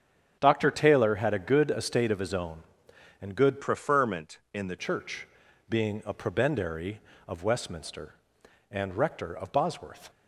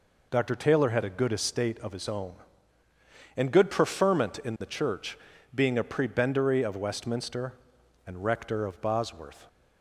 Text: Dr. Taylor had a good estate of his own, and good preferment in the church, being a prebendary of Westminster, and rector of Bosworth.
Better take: second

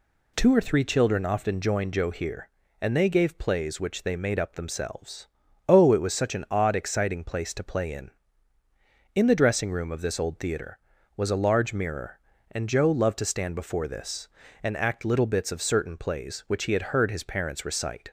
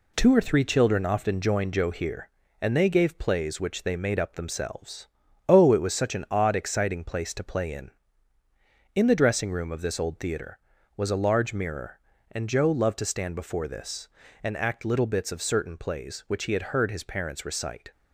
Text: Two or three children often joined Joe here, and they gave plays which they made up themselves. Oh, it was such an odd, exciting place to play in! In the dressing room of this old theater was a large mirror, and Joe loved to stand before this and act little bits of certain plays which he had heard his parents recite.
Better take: first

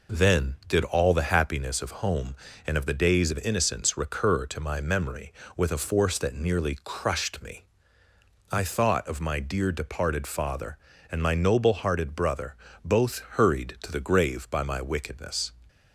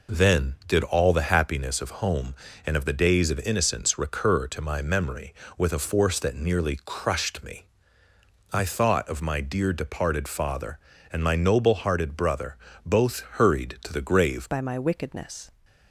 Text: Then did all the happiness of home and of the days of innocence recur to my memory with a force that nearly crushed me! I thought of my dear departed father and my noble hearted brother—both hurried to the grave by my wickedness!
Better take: first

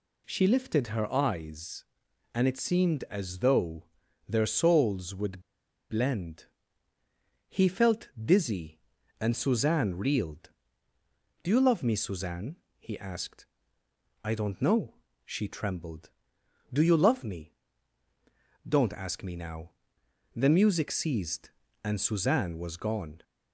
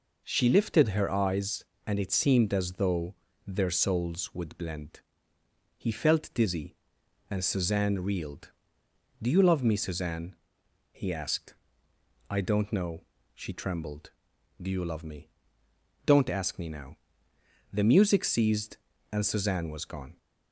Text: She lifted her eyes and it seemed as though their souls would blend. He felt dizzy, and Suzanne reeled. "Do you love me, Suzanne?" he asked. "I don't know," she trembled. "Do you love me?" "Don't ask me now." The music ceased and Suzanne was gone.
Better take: second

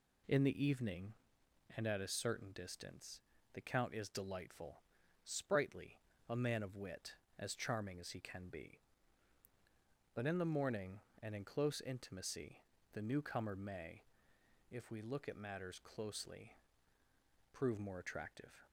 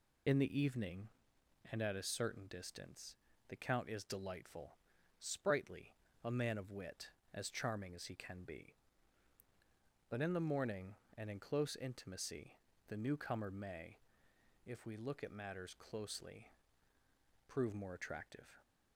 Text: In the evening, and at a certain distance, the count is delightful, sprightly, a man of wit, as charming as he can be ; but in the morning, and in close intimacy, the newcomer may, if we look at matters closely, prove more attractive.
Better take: first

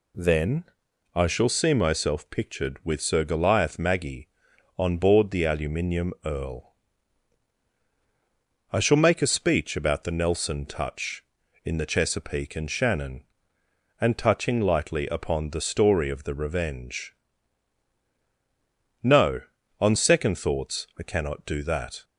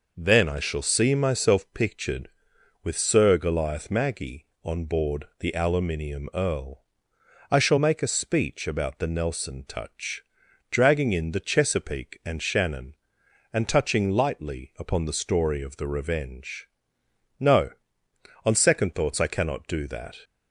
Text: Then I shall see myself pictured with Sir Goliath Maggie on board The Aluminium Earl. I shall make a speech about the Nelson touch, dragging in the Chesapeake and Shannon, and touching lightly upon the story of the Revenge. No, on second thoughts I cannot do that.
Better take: second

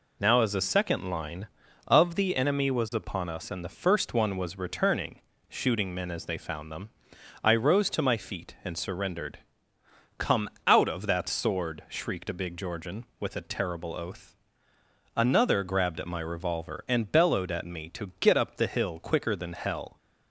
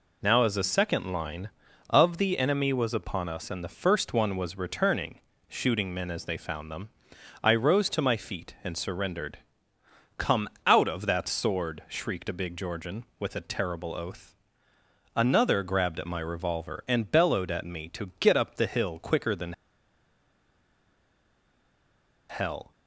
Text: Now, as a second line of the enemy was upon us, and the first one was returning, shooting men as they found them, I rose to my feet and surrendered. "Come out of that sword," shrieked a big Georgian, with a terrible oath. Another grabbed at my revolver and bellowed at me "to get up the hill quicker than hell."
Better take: first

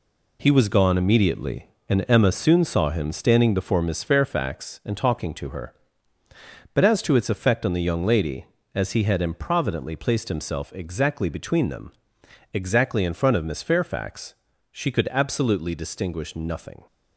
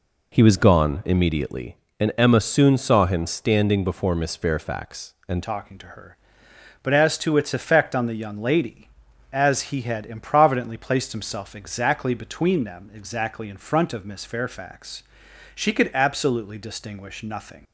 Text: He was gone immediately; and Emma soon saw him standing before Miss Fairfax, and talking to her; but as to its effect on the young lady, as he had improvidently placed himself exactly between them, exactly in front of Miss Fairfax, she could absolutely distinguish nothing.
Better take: first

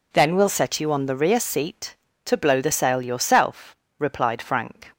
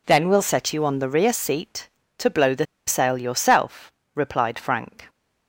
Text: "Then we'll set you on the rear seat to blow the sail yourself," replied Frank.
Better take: first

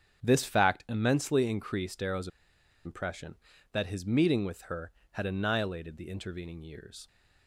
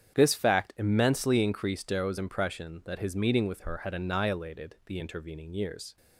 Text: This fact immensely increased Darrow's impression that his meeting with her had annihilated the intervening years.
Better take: second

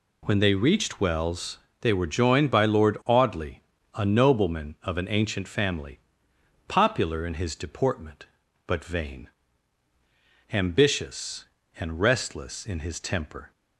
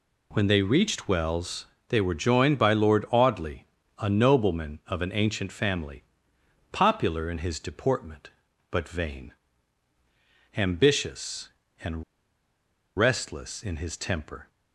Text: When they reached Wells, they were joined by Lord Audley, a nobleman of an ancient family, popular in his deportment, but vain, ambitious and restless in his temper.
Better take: first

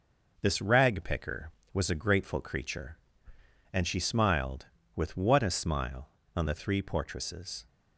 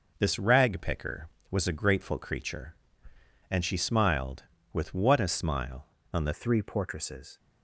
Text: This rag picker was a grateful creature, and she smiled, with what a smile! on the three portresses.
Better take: first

